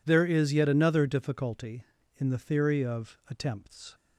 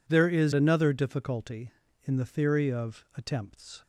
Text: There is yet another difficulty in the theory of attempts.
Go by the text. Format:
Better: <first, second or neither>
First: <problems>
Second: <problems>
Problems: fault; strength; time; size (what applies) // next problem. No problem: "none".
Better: first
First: none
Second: skips "yet"; at 0.5 s